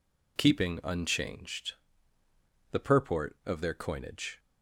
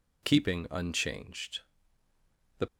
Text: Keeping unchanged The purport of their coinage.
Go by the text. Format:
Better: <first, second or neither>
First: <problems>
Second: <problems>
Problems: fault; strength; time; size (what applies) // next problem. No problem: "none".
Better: first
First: pauses between "unchanged" and "The"; noticeable; at 1.7 s; 0.98 s long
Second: pauses between "unchanged" and "The"; noticeable; at 1.5 s; 0.98 s long // stops before "purport of their coinage"; at 2.6 s